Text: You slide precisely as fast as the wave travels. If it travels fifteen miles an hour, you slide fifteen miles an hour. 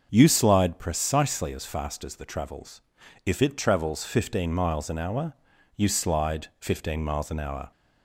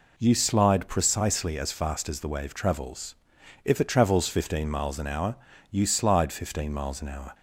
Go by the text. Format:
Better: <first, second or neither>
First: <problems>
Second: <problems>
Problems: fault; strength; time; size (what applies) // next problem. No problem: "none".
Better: second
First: starts louder than the rest; until 1.1 s; 6 dB // skips "wave"; at 2.2 s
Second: none